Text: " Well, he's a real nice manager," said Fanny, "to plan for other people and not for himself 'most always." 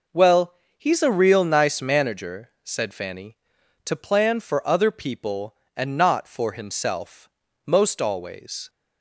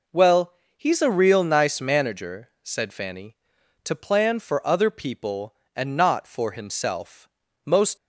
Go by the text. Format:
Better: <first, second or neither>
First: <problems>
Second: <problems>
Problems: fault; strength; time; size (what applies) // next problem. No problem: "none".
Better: first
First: pauses between "himself" and "most"; slight; at 7.2 s; 0.36 s long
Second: pauses between "himself" and "most"; slight; at 7.2 s; 0.36 s long // stops before "always"; at 7.9 s